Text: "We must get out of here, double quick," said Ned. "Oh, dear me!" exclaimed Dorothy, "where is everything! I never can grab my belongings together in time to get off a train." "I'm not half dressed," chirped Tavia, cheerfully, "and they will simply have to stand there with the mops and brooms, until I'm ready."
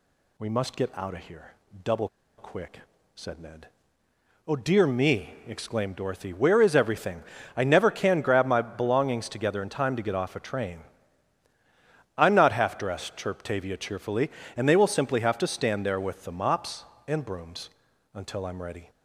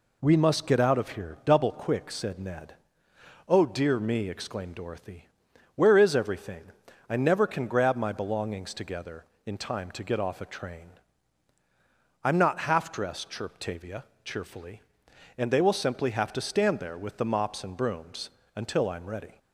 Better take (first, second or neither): second